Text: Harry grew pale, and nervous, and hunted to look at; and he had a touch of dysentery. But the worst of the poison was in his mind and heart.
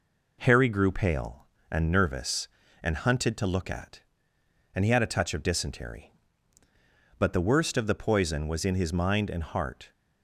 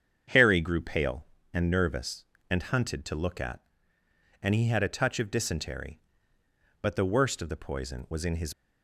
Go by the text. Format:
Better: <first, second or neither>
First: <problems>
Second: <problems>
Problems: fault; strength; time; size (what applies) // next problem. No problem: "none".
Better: first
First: none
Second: starts louder than the rest; strong; until 1.6 s; 7.5 dB // stops before "mind and heart"; at 8.5 s